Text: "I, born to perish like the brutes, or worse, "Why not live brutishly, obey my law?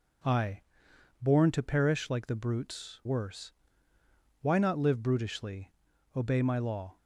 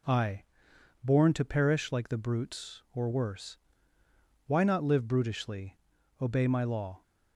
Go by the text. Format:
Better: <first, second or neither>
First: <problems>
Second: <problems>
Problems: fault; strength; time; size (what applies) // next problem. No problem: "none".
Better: second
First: skips "or"; at 3.0 s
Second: none